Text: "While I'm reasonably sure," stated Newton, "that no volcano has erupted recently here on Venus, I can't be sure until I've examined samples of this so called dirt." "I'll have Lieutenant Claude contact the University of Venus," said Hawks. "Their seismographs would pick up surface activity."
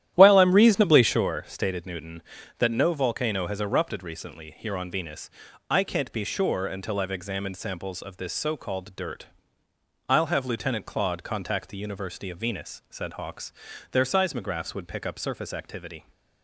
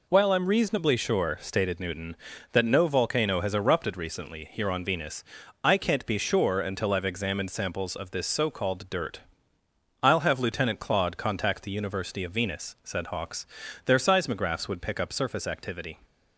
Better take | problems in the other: second | starts louder than the rest; strong; until 1.3 s; 12 dB

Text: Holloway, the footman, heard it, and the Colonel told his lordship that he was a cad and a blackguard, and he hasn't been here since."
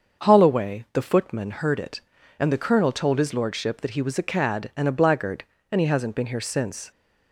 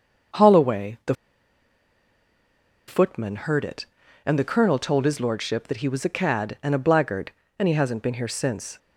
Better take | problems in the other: first | starts louder than the rest; until 3.2 s; 6.5 dB; also in the first // pauses between "the" and "footman"; strong; at 1.1 s; 1.7 s long

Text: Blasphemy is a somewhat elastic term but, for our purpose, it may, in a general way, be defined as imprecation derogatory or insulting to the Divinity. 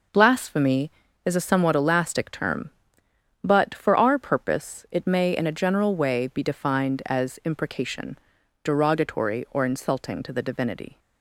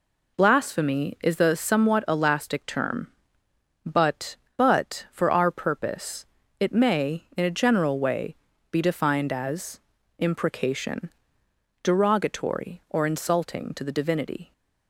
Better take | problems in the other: first | says "but" twice; at 4.5 s // pauses between "as" and "imprecation"; at 9.8 s; 0.38 s long // pauses between "imprecation" and "derogatory"; noticeable; at 11.1 s; 0.72 s long; noticeable in the first

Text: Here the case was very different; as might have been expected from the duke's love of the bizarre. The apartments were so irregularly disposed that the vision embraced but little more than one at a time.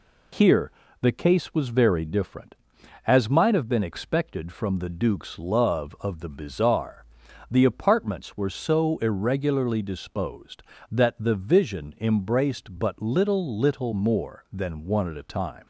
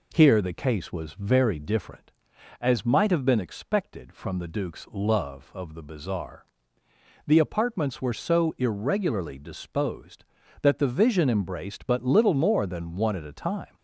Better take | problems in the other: second | pauses between "Here" and "the"; slight; at 0.7 s; 0.30 s long // says "little" twice; at 13.5 s

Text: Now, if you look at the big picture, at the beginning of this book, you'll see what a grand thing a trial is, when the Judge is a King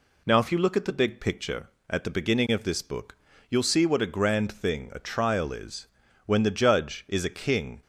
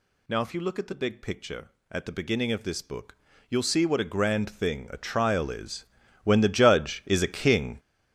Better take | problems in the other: first | gets louder; strong; throughout; 9.5 dB

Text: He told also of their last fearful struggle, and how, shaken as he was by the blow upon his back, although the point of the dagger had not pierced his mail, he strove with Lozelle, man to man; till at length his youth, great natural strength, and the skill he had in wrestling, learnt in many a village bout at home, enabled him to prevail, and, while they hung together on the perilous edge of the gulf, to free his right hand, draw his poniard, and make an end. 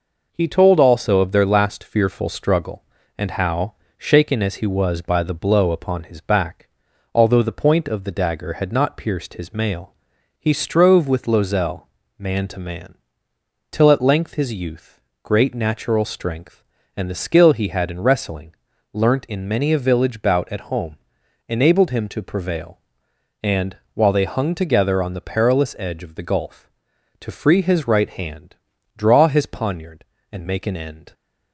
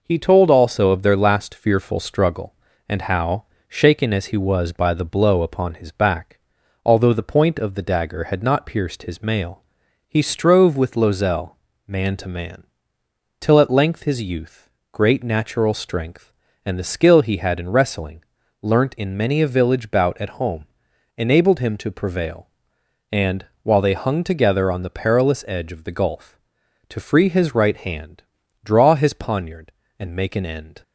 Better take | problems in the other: neither | none

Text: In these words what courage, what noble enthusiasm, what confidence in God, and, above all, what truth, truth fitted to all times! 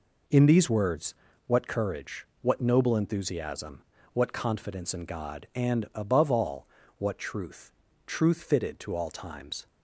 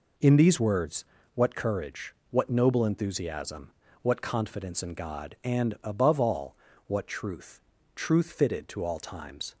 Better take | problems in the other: neither | pauses between "words" and "what"; slight; the same in both

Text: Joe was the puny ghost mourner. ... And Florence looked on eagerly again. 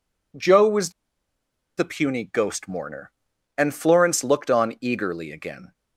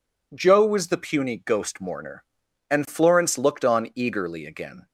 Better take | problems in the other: second | pauses between "was" and "the"; noticeable; at 0.9 s; 0.87 s long

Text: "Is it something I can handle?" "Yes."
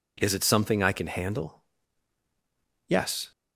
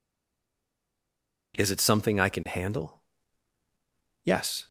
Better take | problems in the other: first | stays silent before the first word; noticeable; until 1.5 s; 1.5 s long

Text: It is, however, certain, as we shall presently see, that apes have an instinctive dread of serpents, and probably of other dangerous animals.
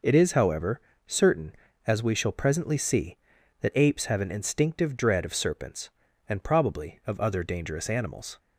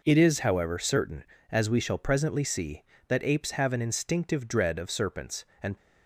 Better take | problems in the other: first | stops before "probably of other dangerous animals"; at 5.7 s

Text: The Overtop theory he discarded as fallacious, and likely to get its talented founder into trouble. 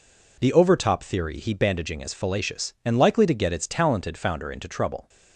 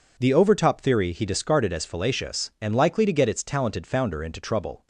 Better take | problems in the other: second | says "bandaging" for "discarded"; at 1.5 s

